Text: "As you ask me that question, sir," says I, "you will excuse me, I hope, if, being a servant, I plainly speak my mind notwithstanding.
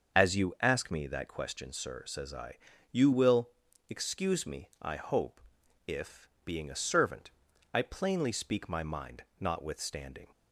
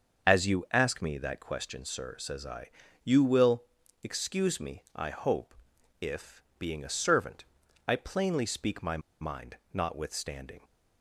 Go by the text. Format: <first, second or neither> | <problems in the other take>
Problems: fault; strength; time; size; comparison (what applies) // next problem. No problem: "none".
first | starts louder than the rest; until 1.3 s; 6.5 dB; also in the first // pauses between "will" and "excuse"; at 3.6 s; 0.38 s long; also in the first // pauses between "my" and "mind"; slight; at 8.9 s; 0.22 s long // pauses between "mind" and "notwithstanding"; slight; at 9.5 s; 0.16 s long; slight in the first